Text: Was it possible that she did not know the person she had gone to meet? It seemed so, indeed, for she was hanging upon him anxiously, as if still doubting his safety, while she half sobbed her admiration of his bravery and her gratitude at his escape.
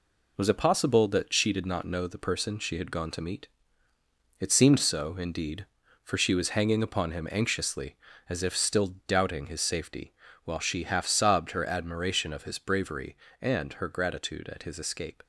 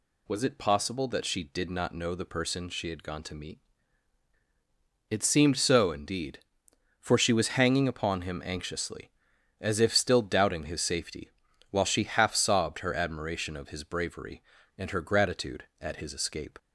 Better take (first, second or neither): second